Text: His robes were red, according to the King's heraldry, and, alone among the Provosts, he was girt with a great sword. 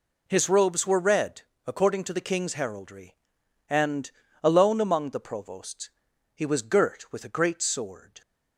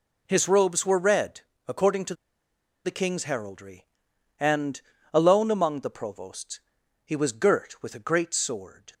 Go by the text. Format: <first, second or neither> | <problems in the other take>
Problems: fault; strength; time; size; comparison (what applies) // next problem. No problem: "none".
first | pauses between "to" and "the"; noticeable; at 2.1 s; 0.71 s long